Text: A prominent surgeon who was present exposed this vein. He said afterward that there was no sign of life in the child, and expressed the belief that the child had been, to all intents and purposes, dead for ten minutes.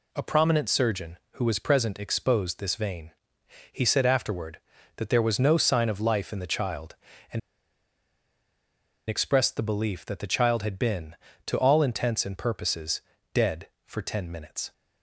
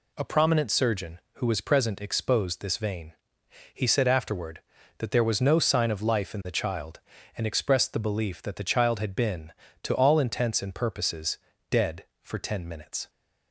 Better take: second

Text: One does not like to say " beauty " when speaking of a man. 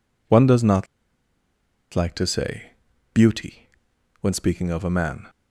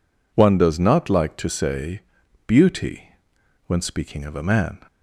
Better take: second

